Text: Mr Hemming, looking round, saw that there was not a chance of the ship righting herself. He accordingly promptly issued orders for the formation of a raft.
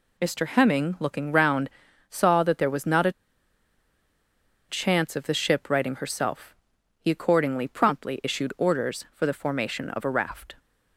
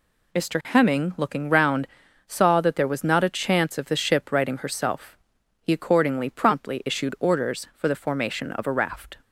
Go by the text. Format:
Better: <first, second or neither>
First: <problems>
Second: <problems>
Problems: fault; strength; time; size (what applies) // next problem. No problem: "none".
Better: second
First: pauses between "a" and "chance"; strong; at 3.1 s; 1.5 s long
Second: none